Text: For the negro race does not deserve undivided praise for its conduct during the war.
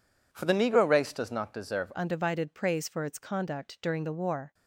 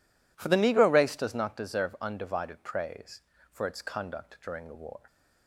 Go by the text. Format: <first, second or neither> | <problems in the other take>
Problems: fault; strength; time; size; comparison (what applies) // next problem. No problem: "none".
second | changes voice at "undivided"; from 1.9 s on; 2.6 s long